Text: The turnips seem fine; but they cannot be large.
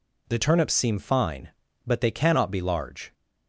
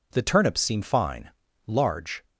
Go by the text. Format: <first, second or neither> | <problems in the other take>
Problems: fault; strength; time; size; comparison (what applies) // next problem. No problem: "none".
first | skips "but they cannot be"; at 1.4 s